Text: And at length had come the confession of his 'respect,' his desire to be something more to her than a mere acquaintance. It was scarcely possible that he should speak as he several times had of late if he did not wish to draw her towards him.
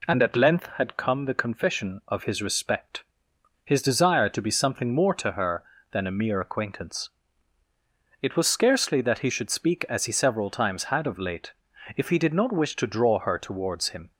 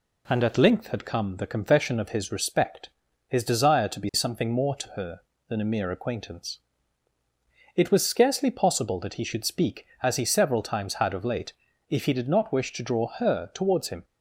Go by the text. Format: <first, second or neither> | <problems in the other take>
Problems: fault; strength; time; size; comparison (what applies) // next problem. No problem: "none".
second | skips "possible"; at 9.0 s // pauses between "late" and "if"; at 11.5 s; 0.44 s long; slight in the second